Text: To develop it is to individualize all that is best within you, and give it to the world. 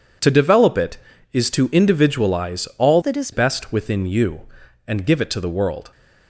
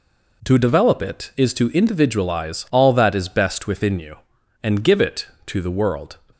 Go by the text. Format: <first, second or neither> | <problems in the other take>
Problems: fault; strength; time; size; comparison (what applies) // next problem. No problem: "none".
second | changes voice from "that" to "is"; from 3.0 to 3.2 s; 0.2 s long